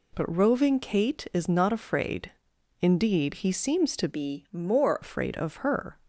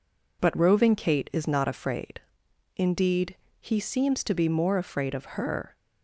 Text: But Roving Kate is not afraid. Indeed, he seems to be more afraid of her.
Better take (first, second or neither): second